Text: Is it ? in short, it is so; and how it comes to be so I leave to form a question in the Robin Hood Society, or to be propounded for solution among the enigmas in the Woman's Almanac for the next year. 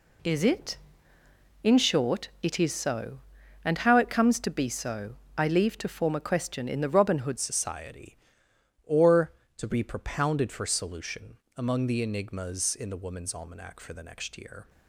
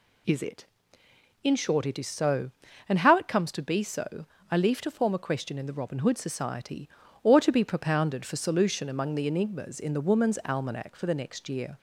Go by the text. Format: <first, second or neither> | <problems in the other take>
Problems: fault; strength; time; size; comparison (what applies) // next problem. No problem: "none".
second | pauses between "so" and "I"; slight; at 5.1 s; 0.20 s long; slight in the second // changes voice at "Society"; from 7.3 s on; 7.3 s long // pauses between "solution" and "among"; slight; at 11.3 s; 0.20 s long